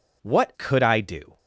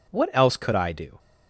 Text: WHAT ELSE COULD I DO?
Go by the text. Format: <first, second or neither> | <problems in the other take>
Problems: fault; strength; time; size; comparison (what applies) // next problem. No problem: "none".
second | skips "ELSE"; at 0.5 s